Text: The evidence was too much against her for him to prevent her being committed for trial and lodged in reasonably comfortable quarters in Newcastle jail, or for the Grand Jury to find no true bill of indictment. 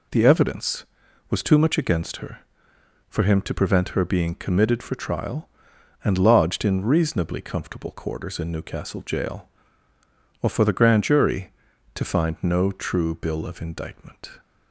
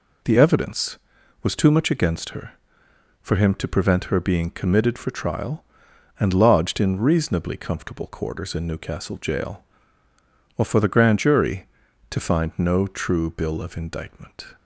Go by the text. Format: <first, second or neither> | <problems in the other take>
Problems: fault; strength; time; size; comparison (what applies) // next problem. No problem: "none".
neither | none